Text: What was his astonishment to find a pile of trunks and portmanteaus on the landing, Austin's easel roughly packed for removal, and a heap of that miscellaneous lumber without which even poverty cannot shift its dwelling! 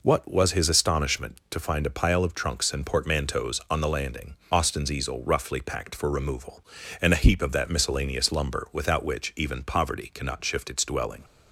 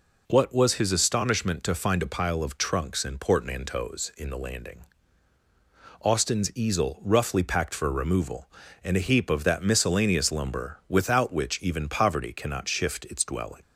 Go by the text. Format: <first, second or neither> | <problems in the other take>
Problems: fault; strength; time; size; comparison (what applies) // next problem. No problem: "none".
first | says "in" for "on"; at 4.1 s